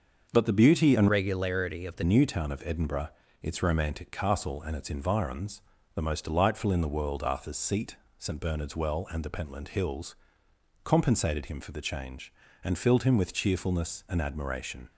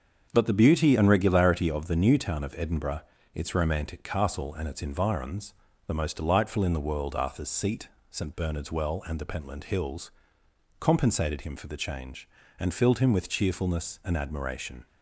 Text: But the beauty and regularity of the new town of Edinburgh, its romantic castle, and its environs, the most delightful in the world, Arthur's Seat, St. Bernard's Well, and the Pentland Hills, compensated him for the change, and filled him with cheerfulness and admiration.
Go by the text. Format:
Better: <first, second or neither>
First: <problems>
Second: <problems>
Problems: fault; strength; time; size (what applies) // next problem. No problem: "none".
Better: second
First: starts louder than the rest; until 1.3 s; 6.5 dB // changes voice from "regularity" to "the"; from 1.0 to 2.0 s; 1.0 s long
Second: starts louder than the rest; until 1.3 s; 7 dB